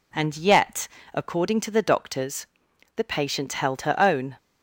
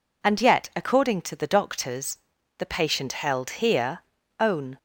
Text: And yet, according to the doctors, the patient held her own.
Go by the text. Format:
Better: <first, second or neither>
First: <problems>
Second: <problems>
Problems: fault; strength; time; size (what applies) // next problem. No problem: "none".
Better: first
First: none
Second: says "here" for "her"; at 3.6 s